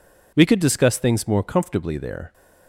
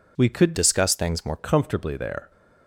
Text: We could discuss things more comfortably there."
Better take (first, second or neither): first